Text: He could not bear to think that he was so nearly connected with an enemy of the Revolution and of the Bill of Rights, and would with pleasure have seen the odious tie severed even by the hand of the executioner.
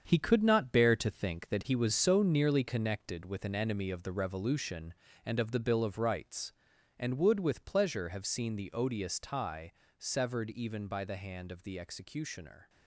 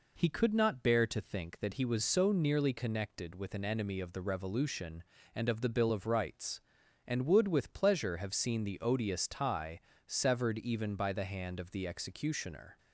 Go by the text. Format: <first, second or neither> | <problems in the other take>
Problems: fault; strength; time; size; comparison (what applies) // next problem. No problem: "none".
second | gets quieter; strong; throughout; 8.5 dB // pauses between "tie" and "severed"; slight; at 9.7 s; 0.26 s long; slight in the second